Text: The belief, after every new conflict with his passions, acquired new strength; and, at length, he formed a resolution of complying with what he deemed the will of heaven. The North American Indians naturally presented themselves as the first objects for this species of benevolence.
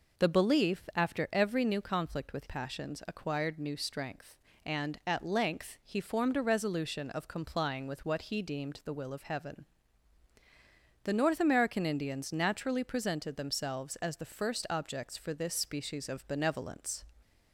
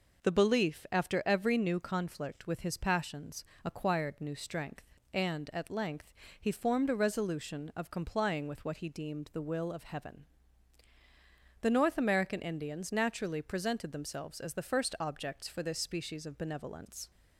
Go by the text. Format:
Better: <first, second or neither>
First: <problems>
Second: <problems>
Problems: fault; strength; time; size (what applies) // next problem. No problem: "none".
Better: second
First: skips "his"; at 2.4 s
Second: none